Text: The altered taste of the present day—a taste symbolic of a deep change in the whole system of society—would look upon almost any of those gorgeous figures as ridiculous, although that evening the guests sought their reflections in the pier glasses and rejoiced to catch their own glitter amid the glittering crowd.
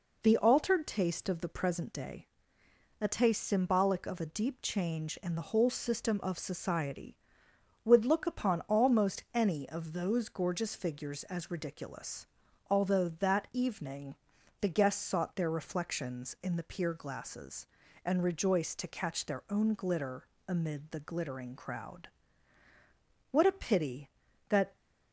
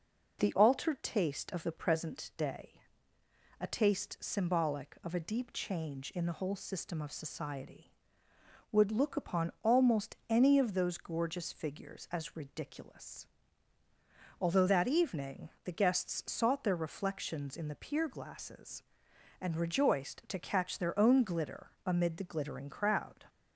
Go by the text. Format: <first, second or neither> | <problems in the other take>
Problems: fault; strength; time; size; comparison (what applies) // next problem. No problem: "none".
second | pauses between "evening" and "the"; at 14.1 s; 0.44 s long; slight in the second // pauses between "glitter" and "amid"; slight; at 20.2 s; 0.22 s long; slight in the second // goes on to say "What a pity that"; from 23.2 s on; 1.4 s long